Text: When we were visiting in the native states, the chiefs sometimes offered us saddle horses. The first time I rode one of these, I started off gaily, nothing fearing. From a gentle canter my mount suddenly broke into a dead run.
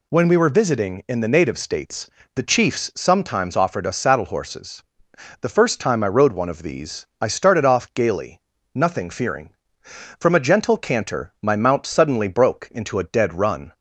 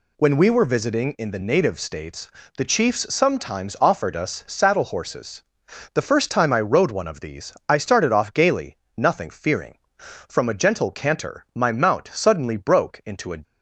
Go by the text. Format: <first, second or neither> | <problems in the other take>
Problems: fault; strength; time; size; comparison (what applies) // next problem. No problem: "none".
first | stops before "dead run"; at 13.4 s